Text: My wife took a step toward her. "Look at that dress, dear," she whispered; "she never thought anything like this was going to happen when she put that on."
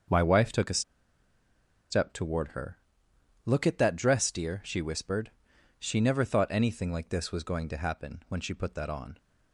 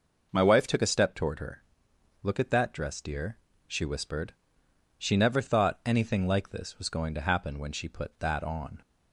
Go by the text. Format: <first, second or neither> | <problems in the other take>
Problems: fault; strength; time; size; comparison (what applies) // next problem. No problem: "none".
second | starts louder than the rest; until 2.1 s; 6.5 dB // pauses between "a" and "step"; at 0.8 s; 1.0 s long